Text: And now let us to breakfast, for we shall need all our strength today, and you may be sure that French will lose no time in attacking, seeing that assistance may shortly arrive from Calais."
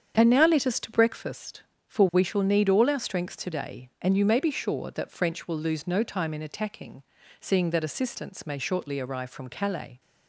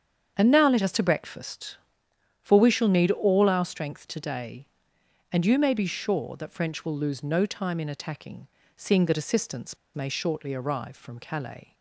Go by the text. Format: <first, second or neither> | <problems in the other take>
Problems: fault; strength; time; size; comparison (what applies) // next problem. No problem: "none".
first | starts louder than the rest; strong; until 1.3 s; 7.5 dB; strong in the first // pauses between "assistance" and "may"; slight; at 9.7 s; 0.18 s long